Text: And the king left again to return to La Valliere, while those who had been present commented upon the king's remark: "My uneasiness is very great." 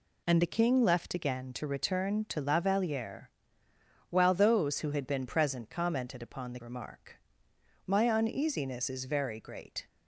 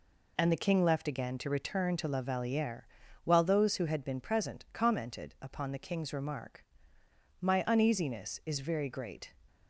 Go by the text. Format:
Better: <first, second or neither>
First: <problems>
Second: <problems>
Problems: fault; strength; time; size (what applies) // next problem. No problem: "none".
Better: second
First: skips "king's"; at 6.6 s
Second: none